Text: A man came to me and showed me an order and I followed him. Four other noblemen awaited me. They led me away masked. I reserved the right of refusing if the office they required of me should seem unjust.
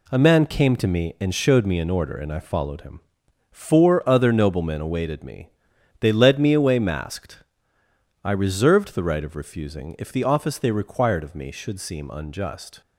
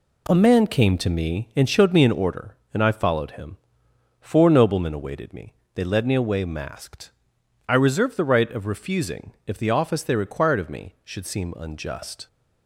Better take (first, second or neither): first